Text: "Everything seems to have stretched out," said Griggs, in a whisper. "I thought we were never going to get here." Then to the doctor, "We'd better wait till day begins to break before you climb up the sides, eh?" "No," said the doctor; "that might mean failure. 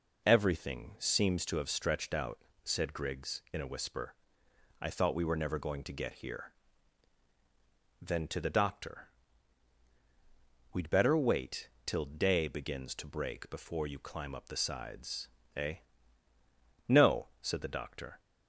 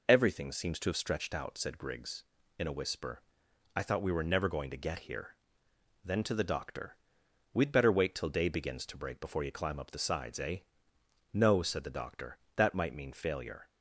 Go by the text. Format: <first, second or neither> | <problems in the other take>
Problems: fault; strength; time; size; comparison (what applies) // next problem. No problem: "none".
second | pauses between "wait" and "till"; slight; at 11.6 s; 0.18 s long // stops before "that might mean failure"; at 18.1 s